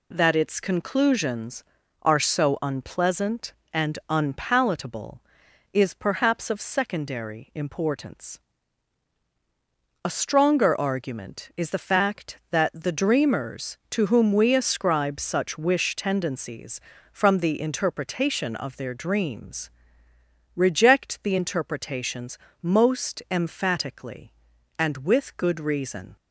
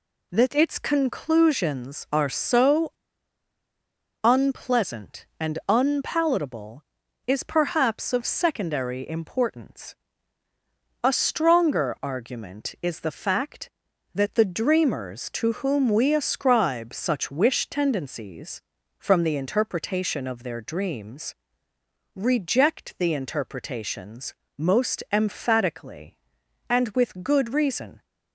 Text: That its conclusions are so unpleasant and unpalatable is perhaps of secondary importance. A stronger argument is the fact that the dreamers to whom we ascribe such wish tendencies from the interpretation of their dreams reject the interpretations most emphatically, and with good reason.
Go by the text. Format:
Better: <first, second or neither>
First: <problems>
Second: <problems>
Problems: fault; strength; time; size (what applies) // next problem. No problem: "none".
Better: first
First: pauses between "dreams" and "reject"; noticeable; at 19.7 s; 0.86 s long // pauses between "interpretations" and "most"; slight; at 22.3 s; 0.28 s long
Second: pauses between "so" and "unpleasant"; strong; at 2.9 s; 1.3 s long // pauses between "dreams" and "reject"; noticeable; at 21.3 s; 0.80 s long // pauses between "interpretations" and "most"; slight; at 24.3 s; 0.24 s long